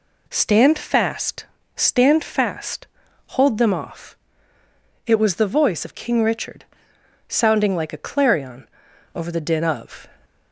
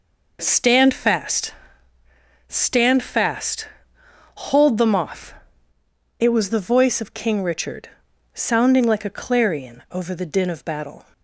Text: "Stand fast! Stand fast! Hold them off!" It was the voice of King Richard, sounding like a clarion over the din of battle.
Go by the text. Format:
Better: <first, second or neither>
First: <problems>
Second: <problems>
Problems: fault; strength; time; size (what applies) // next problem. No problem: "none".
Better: second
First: pauses between "clarion" and "over"; noticeable; at 8.6 s; 0.46 s long // stops before "battle"; at 10.2 s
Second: none